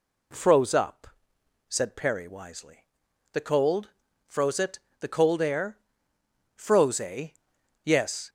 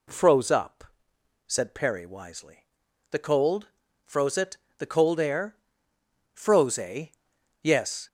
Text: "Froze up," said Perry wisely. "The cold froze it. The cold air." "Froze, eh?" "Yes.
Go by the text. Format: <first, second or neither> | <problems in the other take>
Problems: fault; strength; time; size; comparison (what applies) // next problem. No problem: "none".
neither | pauses between "cold" and "froze"; the same in both